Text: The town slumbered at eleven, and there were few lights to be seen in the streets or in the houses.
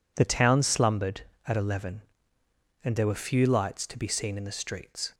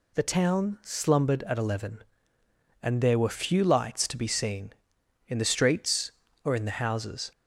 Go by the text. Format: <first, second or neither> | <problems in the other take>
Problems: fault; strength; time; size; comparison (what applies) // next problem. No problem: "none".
second | stops before "or in the houses"; at 5.1 s